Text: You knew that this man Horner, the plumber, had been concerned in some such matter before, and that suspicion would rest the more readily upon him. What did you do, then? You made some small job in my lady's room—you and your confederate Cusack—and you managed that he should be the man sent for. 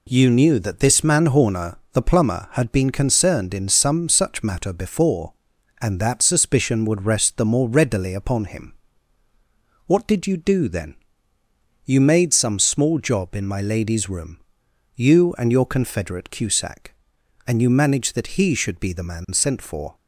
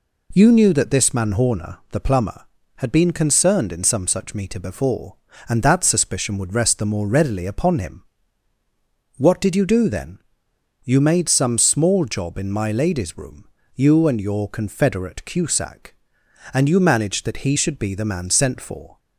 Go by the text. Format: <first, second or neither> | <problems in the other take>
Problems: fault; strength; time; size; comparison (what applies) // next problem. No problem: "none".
first | says "meter" for "matter"; at 4.3 s